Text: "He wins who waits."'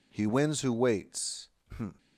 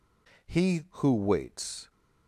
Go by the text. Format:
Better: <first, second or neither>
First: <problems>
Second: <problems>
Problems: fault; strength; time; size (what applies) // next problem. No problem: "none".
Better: first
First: none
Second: skips "wins"; at 0.8 s